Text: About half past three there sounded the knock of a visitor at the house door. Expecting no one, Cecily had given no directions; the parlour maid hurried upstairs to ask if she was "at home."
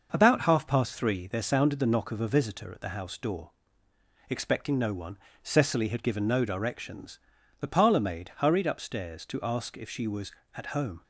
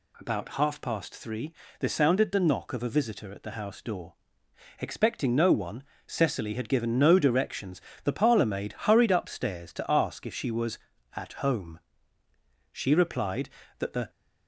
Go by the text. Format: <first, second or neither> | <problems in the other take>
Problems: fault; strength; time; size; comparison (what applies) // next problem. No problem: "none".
first | pauses between "three" and "there"; slight; at 1.5 s; 0.26 s long // goes on to say "She replied that the"; from 12.7 s on; 1.3 s long